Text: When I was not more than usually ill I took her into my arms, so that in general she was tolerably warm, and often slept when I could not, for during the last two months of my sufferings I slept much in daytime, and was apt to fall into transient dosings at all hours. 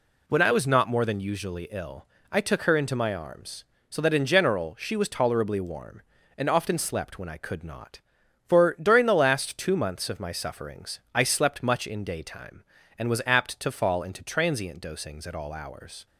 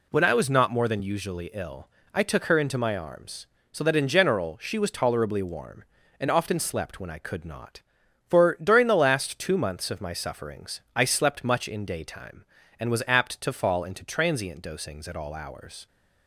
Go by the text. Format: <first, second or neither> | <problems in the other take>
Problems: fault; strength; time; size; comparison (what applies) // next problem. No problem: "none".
neither | pauses between "ill" and "I"; slight; the same in both // pauses between "sufferings" and "I"; slight; the same in both